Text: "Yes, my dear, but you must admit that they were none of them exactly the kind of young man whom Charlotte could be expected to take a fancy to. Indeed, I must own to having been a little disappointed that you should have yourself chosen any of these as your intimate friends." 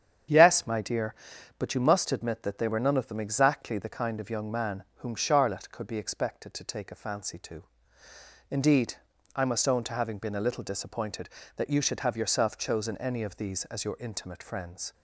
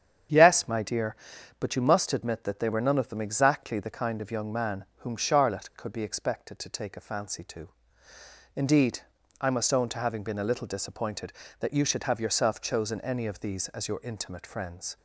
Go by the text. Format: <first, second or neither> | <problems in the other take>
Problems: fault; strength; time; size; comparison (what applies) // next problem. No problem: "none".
neither | starts louder than the rest; strong; the same in both